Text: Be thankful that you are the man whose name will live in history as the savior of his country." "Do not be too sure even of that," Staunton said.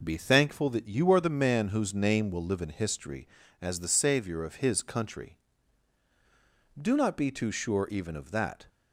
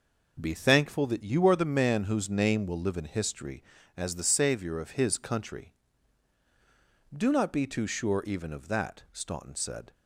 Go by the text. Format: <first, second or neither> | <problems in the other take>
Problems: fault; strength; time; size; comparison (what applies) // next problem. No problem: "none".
second | stops before "Staunton said"; at 8.6 s